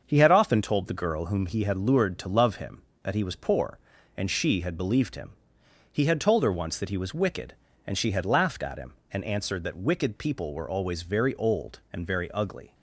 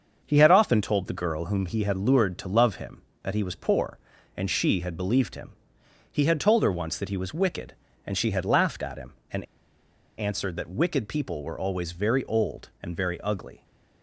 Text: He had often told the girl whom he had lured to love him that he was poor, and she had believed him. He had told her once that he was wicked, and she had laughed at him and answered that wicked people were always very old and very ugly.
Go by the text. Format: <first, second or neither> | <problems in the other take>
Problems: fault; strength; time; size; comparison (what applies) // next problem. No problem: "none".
first | starts louder than the rest; until 1.2 s; 6.5 dB; also in the first // pauses between "and" and "answered"; noticeable; at 9.4 s; 0.75 s long